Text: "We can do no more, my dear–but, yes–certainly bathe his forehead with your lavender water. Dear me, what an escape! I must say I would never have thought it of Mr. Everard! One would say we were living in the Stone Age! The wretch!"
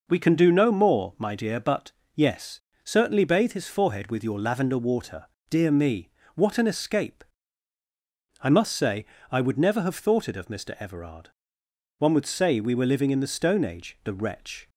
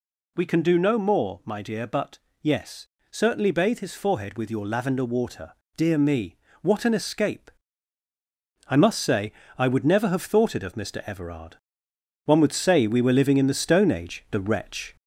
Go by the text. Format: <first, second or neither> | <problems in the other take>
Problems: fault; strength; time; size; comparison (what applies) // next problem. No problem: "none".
first | gets louder; slight; throughout; 2.5 dB // pauses between "say" and "I"; slight; at 9.3 s; 0.26 s long; slight in the first